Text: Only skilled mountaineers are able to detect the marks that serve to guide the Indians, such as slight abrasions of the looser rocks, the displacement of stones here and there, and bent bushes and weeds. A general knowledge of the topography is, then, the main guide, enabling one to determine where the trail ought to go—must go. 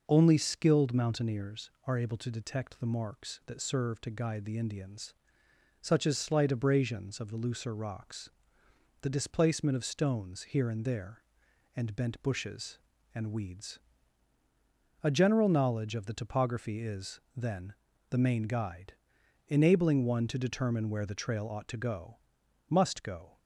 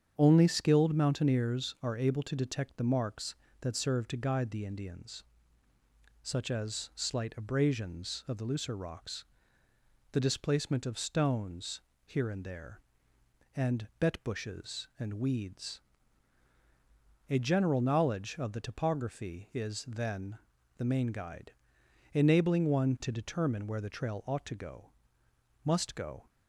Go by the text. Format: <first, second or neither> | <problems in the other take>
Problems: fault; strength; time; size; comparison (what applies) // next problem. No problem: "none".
first | starts louder than the rest; strong; until 1.1 s; 8 dB // pauses between "stones" and "here"; slight; at 11.8 s; 0.24 s long // says "bet" for "bent"; at 13.9 s